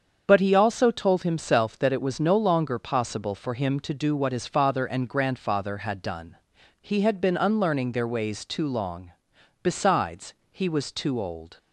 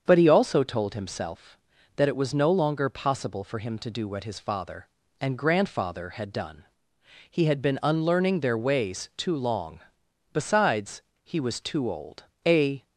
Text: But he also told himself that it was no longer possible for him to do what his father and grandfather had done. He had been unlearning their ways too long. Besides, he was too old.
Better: first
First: starts louder than the rest; strong; until 1.2 s; 7 dB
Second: starts louder than the rest; until 1.0 s; 7 dB // goes on to say "A"; slight; from 12.4 s on; 0.40 s long

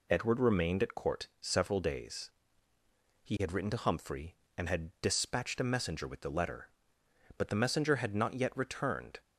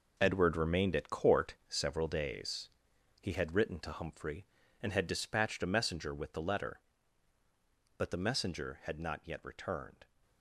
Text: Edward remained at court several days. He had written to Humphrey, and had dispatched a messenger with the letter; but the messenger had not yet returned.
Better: first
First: none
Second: gets quieter; strong; throughout; 10.5 dB // pauses between "court" and "several"; slight; at 1.5 s; 0.16 s long

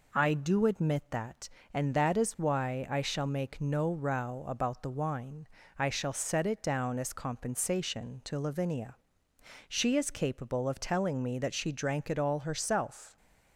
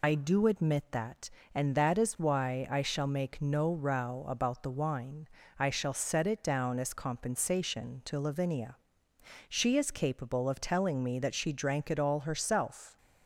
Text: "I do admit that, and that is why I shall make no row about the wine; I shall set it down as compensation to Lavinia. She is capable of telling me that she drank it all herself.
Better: first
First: none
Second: loses the start of "I"; at 0.0 s; 95 ms

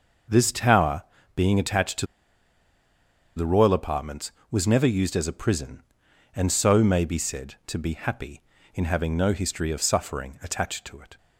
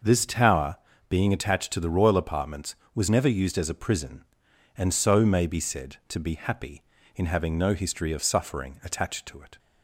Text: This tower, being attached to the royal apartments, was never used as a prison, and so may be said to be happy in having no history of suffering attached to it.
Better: second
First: starts louder than the rest; noticeable; until 1.6 s; 6 dB // pauses between "to" and "the"; strong; at 2.0 s; 1.3 s long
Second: starts louder than the rest; noticeable; until 1.3 s; 6 dB

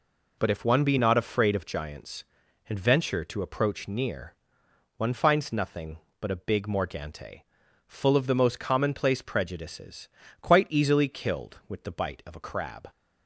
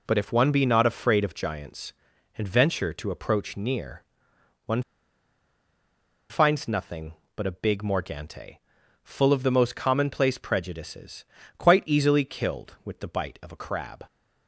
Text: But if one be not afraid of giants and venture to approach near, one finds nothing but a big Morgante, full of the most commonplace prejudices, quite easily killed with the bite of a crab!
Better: first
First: none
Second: pauses between "one" and "finds"; strong; at 4.8 s; 1.4 s long

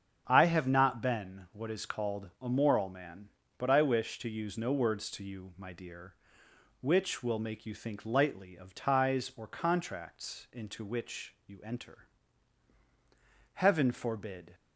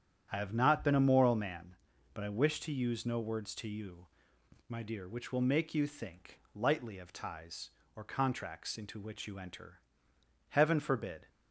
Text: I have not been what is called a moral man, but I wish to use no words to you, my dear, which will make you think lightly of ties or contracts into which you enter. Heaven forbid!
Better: first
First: starts louder than the rest; strong; until 1.2 s; 8 dB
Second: starts louder than the rest; strong; until 1.3 s; 9.5 dB // skips "what is called"; at 0.9 s // pauses between "think" and "lightly"; slight; at 6.3 s; 0.16 s long

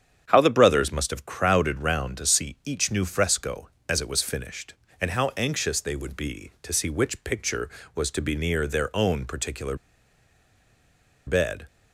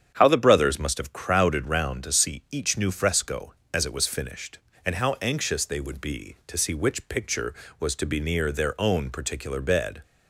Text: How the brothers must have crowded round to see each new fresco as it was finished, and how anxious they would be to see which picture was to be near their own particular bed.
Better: second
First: starts louder than the rest; strong; until 1.2 s; 8.5 dB // pauses between "particular" and "bed"; strong; at 9.7 s; 1.5 s long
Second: starts louder than the rest; strong; until 1.1 s; 8.5 dB

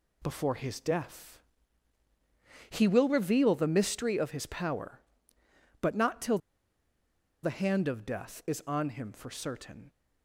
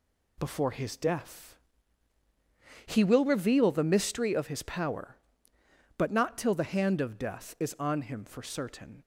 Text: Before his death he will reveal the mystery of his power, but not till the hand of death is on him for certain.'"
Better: second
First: pauses between "death" and "he"; strong; at 1.4 s; 1.3 s long // pauses between "till" and "the"; at 6.3 s; 1.0 s long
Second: pauses between "death" and "he"; strong; at 1.5 s; 1.3 s long

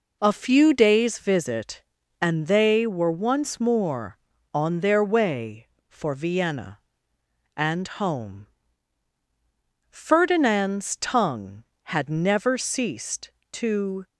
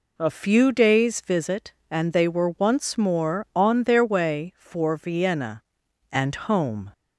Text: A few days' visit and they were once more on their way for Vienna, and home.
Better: second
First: goes on to say "Ferdinand's tongue had never ceased to"; strong; from 9.9 s on; 4.1 s long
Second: none

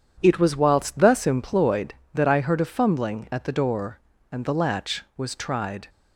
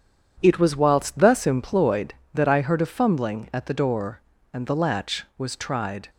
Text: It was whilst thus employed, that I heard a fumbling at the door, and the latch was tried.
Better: neither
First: starts louder than the rest; strong; until 1.2 s; 8.5 dB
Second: starts louder than the rest; strong; until 1.4 s; 8.5 dB

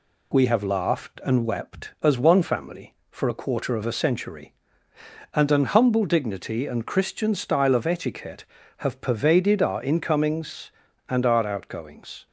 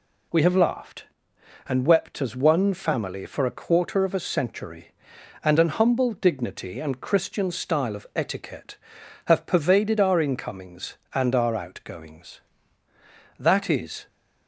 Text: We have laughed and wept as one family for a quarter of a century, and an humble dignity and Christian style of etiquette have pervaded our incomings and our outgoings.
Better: first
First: none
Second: goes on to say "That is"; noticeable; from 13.3 s on; 0.70 s long

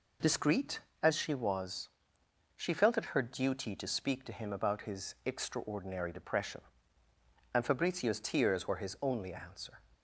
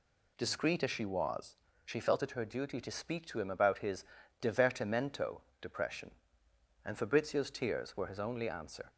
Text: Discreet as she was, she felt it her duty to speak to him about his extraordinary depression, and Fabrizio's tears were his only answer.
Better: first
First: none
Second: says "divertimento" for "extraordinary"; at 4.4 s

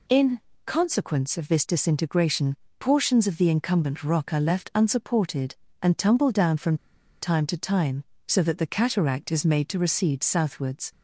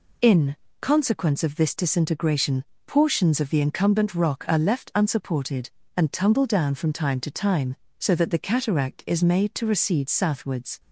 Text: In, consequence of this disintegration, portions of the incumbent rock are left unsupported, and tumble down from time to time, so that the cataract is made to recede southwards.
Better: second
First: pauses between "from" and "time"; at 6.7 s; 0.45 s long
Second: none

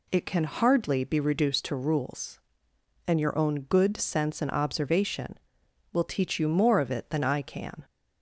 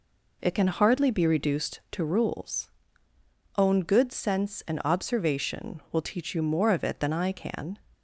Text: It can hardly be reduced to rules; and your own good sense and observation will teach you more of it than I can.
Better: first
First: none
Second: skips "and your"; at 3.1 s

